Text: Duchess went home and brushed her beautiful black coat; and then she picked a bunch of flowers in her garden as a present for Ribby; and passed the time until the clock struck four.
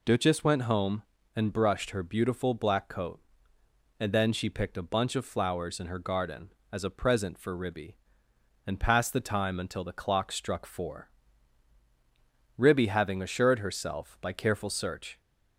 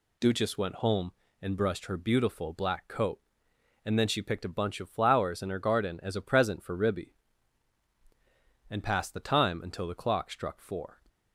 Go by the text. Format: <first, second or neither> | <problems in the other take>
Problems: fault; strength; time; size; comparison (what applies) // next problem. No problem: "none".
second | goes on to say "Ribby having assured herself by careful search"; strong; from 12.5 s on; 2.6 s long